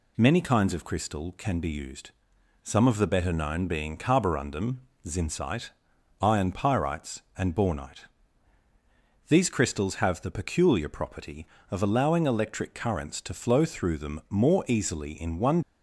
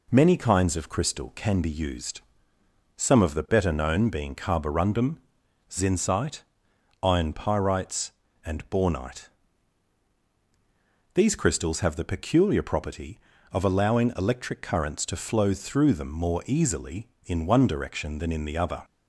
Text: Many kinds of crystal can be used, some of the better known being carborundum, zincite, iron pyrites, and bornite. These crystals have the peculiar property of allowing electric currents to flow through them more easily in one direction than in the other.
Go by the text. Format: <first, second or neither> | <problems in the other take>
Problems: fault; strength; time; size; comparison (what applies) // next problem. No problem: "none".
second | stops before "direction than in the other"; at 15.6 s